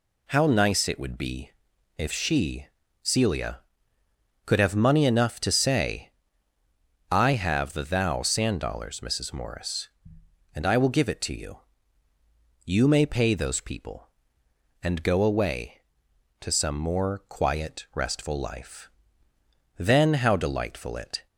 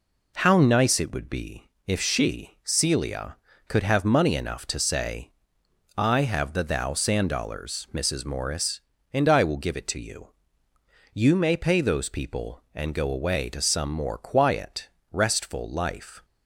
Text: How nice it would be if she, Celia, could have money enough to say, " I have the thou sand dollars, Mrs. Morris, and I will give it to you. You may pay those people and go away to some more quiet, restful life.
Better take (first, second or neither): second